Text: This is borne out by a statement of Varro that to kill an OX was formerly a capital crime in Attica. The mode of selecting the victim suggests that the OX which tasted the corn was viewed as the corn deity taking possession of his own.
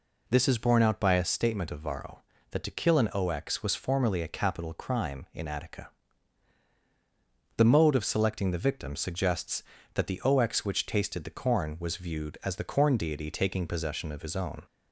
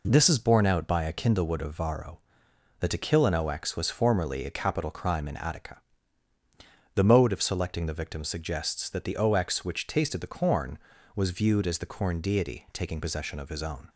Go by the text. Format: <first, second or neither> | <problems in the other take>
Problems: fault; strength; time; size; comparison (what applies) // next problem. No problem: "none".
first | says "kindlewood" for "statement"; at 1.1 s